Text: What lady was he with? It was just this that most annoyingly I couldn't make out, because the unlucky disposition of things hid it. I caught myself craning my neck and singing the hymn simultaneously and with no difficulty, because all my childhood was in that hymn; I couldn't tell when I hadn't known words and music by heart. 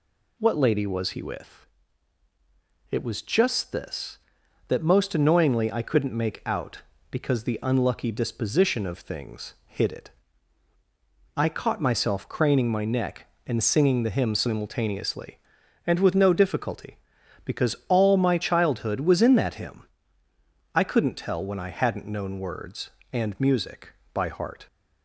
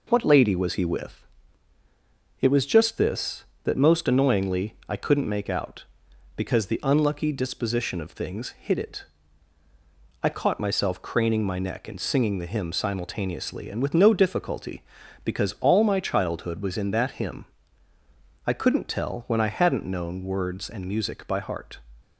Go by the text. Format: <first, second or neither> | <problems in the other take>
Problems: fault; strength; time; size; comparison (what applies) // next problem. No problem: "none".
neither | none